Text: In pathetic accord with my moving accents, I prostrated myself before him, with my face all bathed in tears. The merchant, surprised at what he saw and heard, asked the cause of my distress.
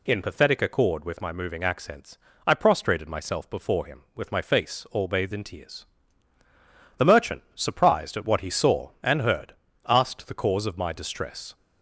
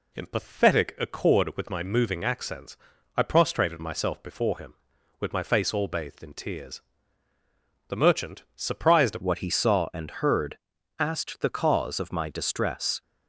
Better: first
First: none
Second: changes voice at "what"; from 9.2 s on; 3.8 s long

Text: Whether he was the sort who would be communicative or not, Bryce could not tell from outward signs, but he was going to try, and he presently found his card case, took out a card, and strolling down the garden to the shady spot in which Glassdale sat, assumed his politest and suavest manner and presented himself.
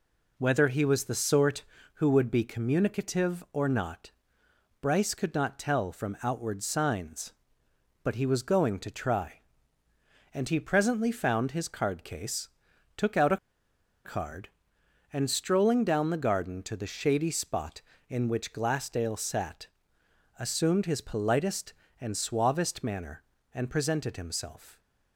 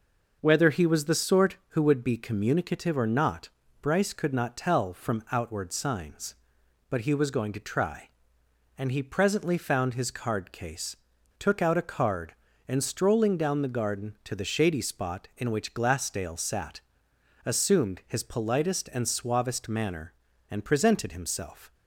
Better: second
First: pauses between "a" and "card"; noticeable; at 13.3 s; 0.68 s long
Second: none

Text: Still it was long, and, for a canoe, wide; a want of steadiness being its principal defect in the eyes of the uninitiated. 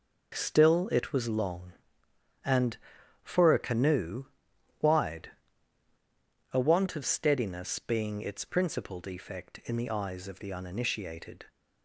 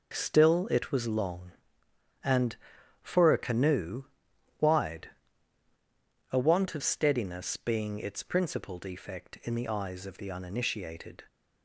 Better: neither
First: none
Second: none

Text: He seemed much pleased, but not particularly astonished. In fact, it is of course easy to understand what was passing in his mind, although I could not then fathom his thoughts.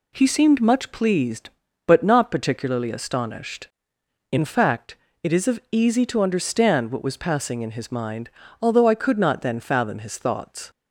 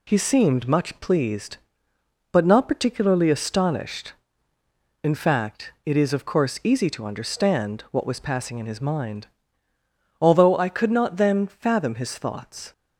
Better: second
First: skips "course"; at 5.6 s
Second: none

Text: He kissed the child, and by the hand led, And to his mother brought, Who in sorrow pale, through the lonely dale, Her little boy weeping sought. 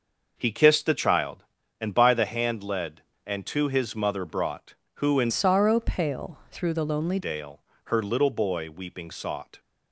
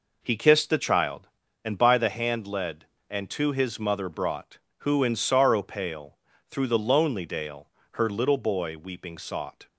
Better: second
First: changes voice from "sorrow" to "lonely"; from 5.2 to 7.1 s; 1.9 s long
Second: none

